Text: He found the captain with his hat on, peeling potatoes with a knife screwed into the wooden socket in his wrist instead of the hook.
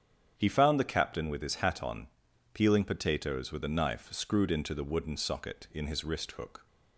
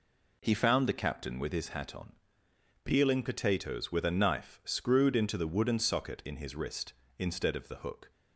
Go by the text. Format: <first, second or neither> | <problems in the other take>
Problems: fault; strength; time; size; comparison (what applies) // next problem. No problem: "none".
second | starts louder than the rest; strong; until 1.3 s; 8.5 dB // skips "instead of the"; at 6.3 s